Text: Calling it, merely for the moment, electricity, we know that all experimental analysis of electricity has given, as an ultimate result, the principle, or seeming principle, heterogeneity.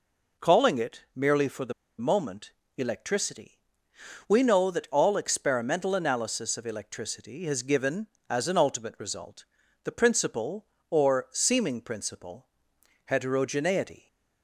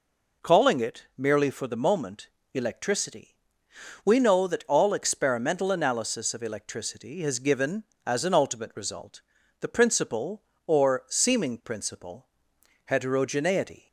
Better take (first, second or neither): second